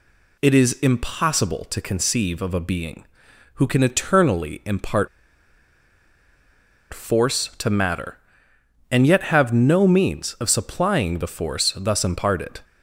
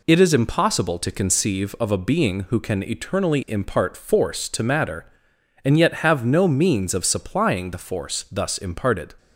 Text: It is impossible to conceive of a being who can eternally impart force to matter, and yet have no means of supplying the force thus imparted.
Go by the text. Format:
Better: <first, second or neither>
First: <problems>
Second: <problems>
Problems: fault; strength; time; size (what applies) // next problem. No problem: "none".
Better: second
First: pauses between "impart" and "force"; strong; at 5.0 s; 1.8 s long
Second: none